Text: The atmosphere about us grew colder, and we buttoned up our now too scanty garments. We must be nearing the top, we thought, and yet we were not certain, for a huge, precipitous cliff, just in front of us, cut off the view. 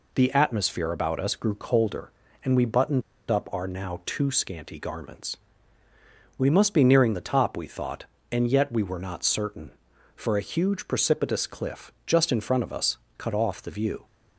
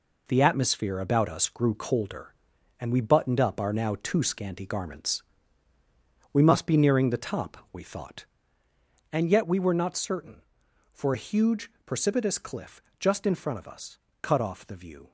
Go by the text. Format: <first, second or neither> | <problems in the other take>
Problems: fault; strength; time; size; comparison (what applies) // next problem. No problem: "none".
second | pauses between "buttoned" and "up"; slight; at 3.0 s; 0.29 s long